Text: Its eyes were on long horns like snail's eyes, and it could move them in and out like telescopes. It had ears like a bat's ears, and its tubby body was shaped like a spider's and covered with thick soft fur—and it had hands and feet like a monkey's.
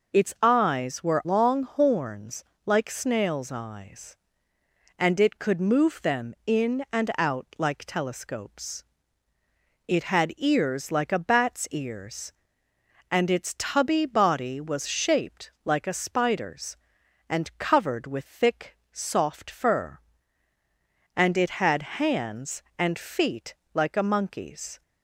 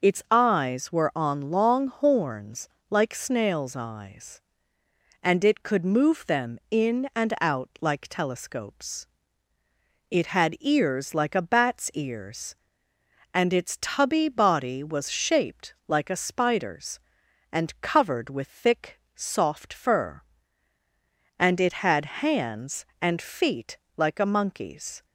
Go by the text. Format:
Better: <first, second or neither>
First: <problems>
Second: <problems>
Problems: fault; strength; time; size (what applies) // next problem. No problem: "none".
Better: second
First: skips "on"; at 1.2 s // pauses between "horns" and "like"; slight; at 2.4 s; 0.22 s long // pauses between "thick" and "soft"; slight; at 18.7 s; 0.16 s long // pauses between "feet" and "like"; slight; at 23.5 s; 0.20 s long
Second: pauses between "horns" and "like"; slight; at 2.6 s; 0.22 s long // pauses between "thick" and "soft"; slight; at 18.9 s; 0.16 s long // pauses between "feet" and "like"; slight; at 23.7 s; 0.20 s long